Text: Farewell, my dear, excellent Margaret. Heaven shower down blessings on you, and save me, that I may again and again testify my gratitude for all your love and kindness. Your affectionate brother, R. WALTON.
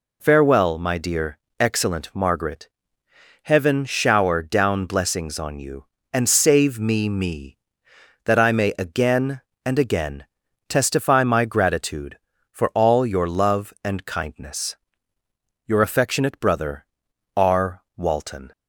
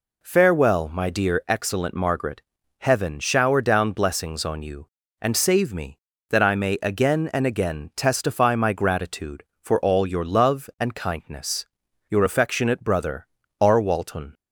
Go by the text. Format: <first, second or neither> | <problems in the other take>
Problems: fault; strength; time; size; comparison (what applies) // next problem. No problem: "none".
second | says "me" twice; at 7.0 s // pauses between "again" and "testify"; at 10.2 s; 0.42 s long